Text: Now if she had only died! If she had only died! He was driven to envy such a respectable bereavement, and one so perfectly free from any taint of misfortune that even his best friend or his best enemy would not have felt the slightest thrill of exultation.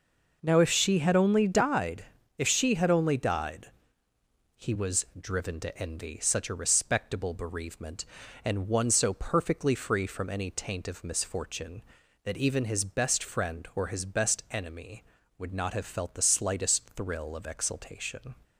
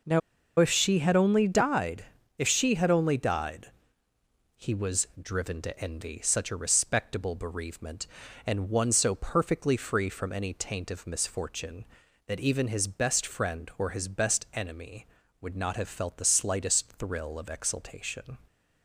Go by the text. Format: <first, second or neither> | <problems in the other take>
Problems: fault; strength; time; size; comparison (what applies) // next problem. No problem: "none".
first | pauses between "Now" and "if"; at 0.2 s; 0.39 s long